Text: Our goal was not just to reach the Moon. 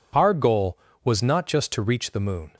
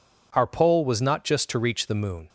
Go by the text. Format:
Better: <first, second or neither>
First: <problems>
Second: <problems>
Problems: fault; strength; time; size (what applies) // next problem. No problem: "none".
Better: first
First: none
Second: says "pole" for "goal"; at 0.4 s